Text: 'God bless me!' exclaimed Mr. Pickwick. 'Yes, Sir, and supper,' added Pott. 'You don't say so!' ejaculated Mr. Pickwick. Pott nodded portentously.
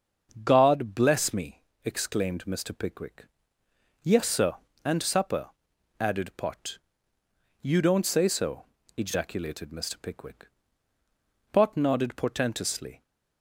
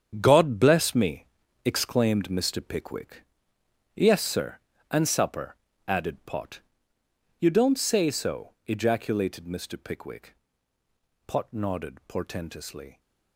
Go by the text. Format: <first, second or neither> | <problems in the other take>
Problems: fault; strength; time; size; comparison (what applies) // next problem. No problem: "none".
first | gets quieter; strong; throughout; 12 dB // starts louder than the rest; strong; until 1.2 s; 8 dB; also in the first